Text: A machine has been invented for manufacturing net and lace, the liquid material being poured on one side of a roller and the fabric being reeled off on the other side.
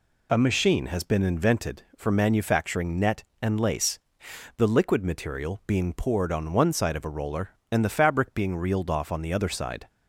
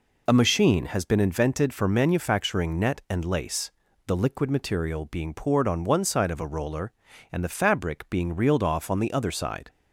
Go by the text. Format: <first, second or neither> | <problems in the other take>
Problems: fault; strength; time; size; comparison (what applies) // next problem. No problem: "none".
neither | none